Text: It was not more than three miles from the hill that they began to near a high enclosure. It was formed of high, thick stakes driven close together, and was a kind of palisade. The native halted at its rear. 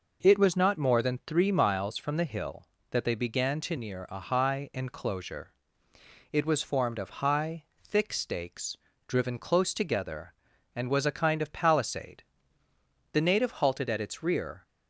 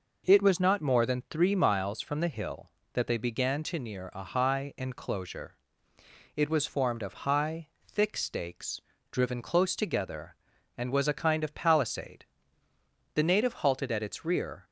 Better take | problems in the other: neither | pauses between "stakes" and "driven"; slight; the same in both

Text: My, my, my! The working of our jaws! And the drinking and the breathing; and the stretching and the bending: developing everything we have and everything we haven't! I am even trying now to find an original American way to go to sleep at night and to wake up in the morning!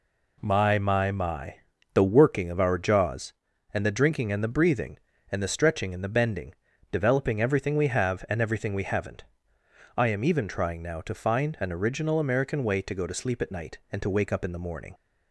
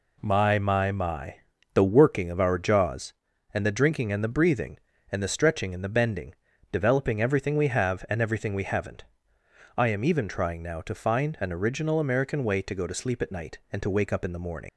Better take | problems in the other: first | leaves "morning" unfinished; at 14.6 s; 50 ms

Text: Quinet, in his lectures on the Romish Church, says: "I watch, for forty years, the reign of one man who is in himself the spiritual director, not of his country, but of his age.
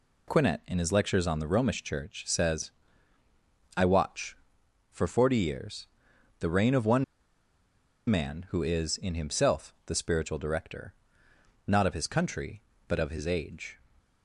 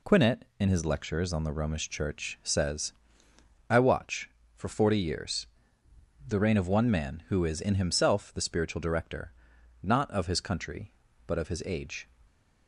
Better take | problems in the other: second | pauses between "one" and "man"; at 7.0 s; 1.0 s long

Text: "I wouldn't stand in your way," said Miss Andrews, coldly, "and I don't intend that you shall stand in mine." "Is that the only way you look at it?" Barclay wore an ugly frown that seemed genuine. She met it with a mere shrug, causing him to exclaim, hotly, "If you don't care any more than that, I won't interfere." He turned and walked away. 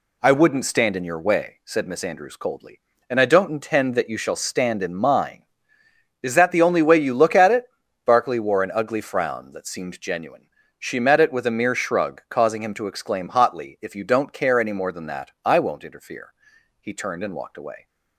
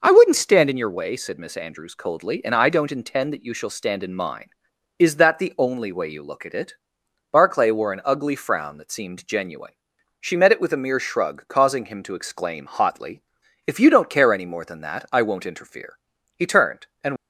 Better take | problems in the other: first | stops before "walked away"; at 17.1 s

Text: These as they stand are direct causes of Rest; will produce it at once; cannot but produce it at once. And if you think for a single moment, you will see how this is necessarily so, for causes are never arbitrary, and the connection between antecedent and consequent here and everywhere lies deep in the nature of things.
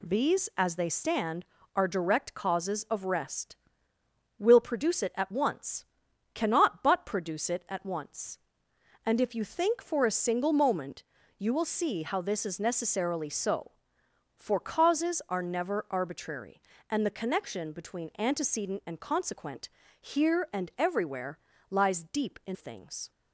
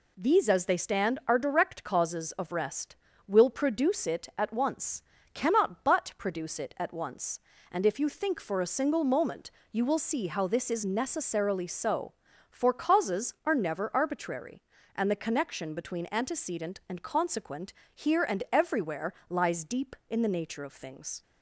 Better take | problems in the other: second | pauses between "consequent" and "here"; slight; at 19.6 s; 0.30 s long; slight in the second // pauses between "everywhere" and "lies"; slight; at 21.3 s; 0.32 s long; slight in the second // skips "the nature of"; at 22.5 s

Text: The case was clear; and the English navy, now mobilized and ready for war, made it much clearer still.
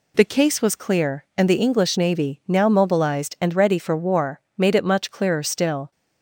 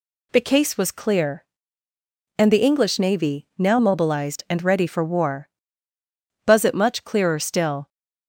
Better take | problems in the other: first | says "buzz" for "made"; at 6.4 s

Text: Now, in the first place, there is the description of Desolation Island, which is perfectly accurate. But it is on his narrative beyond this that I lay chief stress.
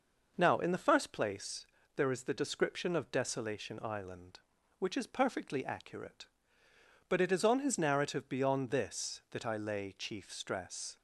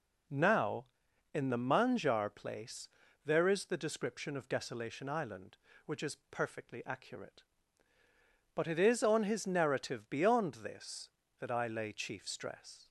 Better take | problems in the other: first | says "manjar" for "first"; at 1.5 s

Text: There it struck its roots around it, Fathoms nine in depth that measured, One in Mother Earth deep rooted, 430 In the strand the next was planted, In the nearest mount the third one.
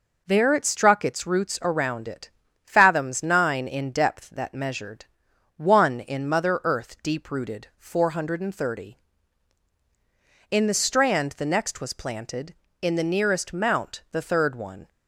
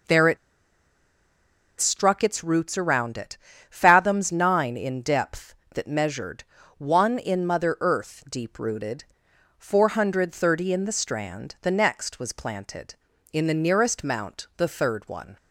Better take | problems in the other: first | pauses between "it" and "struck"; strong; at 0.3 s; 1.4 s long

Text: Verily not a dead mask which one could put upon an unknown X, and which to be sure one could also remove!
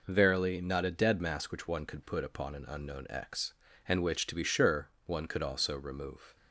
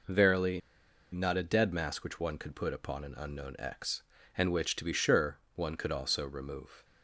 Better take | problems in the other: first | pauses between "Verily" and "not"; noticeable; at 0.6 s; 0.52 s long // pauses between "sure" and "one"; slight; at 5.3 s; 0.16 s long; slight in the first

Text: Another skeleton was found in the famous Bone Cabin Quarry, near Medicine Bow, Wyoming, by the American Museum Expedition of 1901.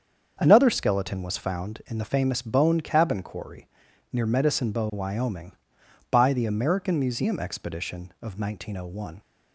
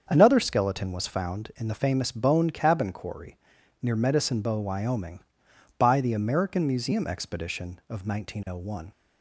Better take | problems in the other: neither | starts louder than the rest; strong; the same in both

